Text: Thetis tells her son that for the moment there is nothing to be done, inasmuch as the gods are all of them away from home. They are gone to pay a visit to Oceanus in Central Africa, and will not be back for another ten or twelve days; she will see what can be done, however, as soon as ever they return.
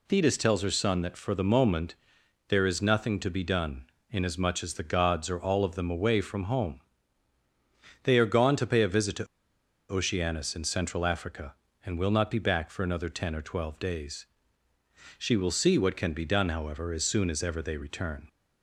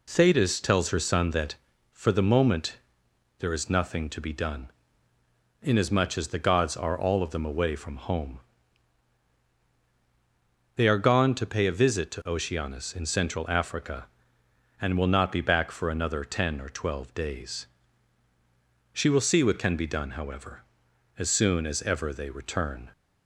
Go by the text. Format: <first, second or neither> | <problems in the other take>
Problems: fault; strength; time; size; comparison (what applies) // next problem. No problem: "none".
second | pauses between "moment" and "there"; noticeable; at 1.9 s; 0.54 s long; noticeable in the second // pauses between "to" and "Oceanus"; noticeable; at 9.2 s; 0.65 s long